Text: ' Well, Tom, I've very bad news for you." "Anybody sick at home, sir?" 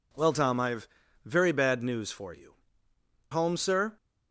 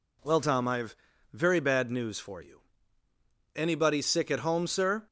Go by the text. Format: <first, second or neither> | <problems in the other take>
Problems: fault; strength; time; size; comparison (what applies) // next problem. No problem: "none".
second | pauses between "I've" and "very"; slight; at 0.8 s; 0.36 s long; slight in the second // skips "Anybody sick at"; at 2.9 s